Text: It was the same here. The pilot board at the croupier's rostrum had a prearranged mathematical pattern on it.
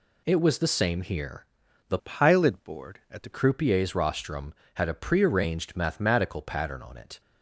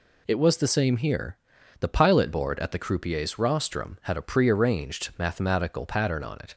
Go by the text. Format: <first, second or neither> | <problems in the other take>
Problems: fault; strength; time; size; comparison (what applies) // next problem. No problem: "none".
second | changes voice from "pilot" to "the"; from 1.9 to 3.3 s; 1.4 s long